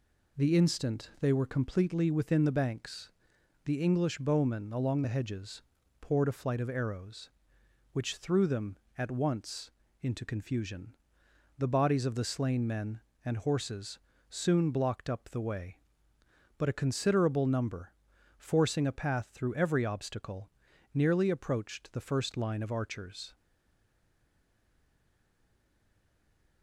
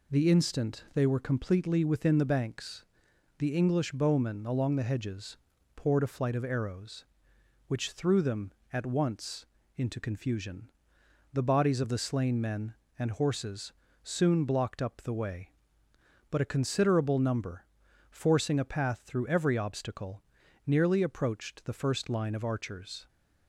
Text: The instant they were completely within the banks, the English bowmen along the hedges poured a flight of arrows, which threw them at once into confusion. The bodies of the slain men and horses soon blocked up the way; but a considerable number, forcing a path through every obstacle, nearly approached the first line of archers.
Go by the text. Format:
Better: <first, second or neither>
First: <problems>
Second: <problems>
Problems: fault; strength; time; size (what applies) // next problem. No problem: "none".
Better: second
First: pauses between "hedges" and "poured"; at 5.6 s; 0.40 s long // pauses between "once" and "into"; slight; at 9.6 s; 0.32 s long // pauses between "horses" and "soon"; slight; at 13.9 s; 0.28 s long // stays silent after the last word; strong; from 23.3 s on; 3.3 s long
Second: pauses between "hedges" and "poured"; at 5.3 s; 0.40 s long // pauses between "once" and "into"; slight; at 9.4 s; 0.32 s long // pauses between "horses" and "soon"; slight; at 13.7 s; 0.28 s long